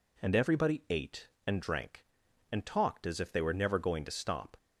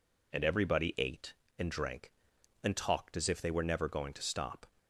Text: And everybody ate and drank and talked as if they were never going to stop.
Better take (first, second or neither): neither